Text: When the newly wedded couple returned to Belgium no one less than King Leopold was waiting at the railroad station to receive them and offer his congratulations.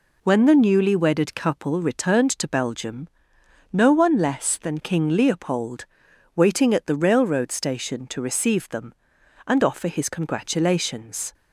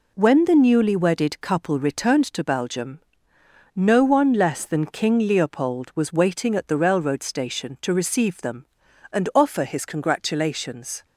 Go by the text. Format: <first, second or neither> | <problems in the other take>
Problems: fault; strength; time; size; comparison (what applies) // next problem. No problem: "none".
second | pauses between "Belgium" and "no"; noticeable; at 3.0 s; 0.64 s long; noticeable in the second // skips "was"; at 6.1 s